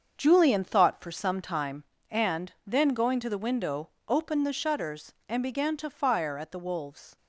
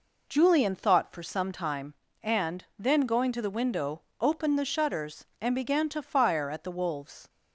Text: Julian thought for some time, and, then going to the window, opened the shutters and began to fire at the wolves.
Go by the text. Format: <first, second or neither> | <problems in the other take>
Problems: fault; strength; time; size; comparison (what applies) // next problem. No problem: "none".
second | gets quieter; strong; throughout; 8.5 dB